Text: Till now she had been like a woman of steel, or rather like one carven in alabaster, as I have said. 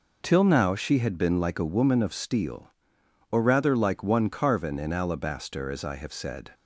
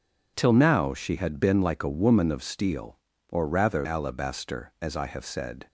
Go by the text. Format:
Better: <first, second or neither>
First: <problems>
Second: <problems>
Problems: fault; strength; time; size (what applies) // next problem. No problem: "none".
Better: first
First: none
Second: skips "like one carven in"; at 3.8 s